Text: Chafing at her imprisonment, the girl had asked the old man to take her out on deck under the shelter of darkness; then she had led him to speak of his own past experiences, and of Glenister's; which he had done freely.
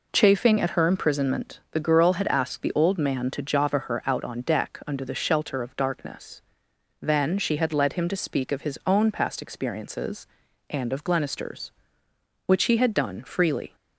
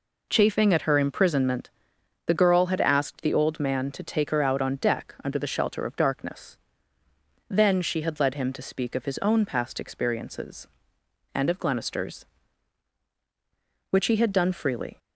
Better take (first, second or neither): second